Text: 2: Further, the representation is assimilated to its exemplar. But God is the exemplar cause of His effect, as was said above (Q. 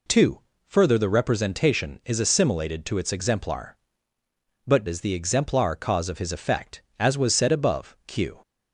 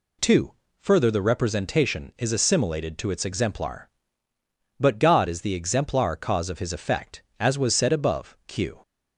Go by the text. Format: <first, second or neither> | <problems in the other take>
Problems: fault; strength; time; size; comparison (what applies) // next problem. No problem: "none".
second | skips "God"; at 4.8 s